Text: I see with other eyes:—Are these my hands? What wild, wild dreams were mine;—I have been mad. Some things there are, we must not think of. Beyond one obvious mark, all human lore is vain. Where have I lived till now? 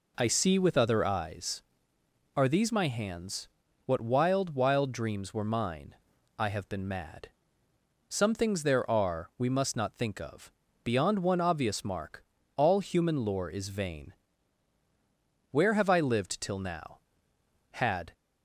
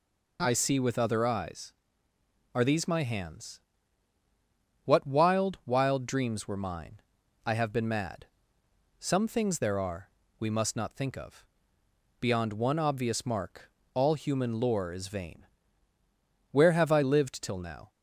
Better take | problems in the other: second | goes on to say "Had"; slight; from 17.7 s on; 0.42 s long

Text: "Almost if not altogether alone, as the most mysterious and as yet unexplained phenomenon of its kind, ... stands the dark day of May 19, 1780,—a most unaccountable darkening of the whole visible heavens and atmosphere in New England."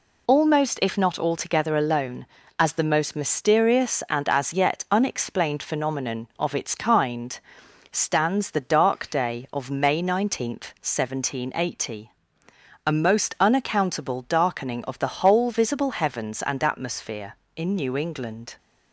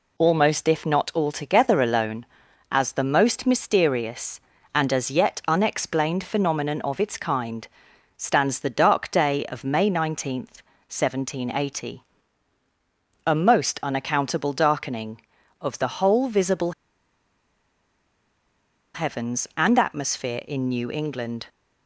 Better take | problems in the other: first | pauses between "visible" and "heavens"; strong; at 16.7 s; 2.2 s long

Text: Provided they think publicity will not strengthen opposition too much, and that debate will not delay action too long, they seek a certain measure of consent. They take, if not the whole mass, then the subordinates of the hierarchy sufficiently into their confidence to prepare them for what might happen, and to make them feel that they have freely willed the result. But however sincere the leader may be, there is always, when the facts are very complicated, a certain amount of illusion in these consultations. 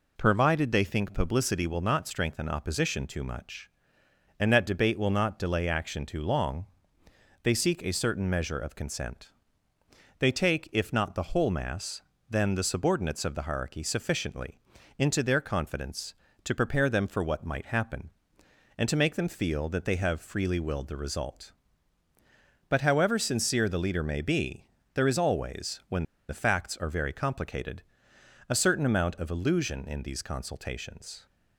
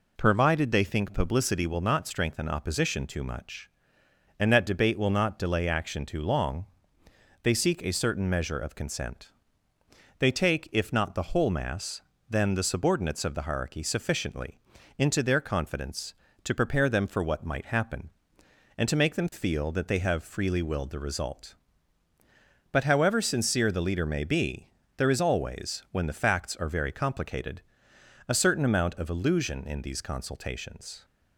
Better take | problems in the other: second | pauses between "sufficiently" and "into"; at 14.5 s; 0.40 s long; also in the second // pauses between "when" and "the"; slight; at 26.0 s; 0.24 s long

